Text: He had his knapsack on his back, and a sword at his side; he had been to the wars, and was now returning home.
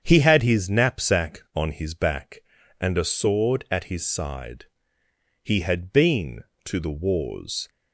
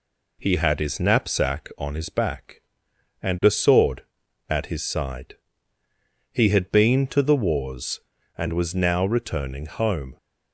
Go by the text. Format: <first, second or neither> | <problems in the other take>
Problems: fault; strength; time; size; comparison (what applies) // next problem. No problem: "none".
second | starts louder than the rest; strong; until 1.0 s; 8 dB // stops before "and was now returning home"; at 7.6 s